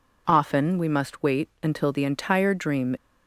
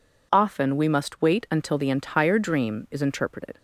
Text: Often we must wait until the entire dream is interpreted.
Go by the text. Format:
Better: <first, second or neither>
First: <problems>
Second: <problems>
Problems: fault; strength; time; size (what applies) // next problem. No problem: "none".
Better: second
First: stops before "is interpreted"; at 2.9 s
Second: none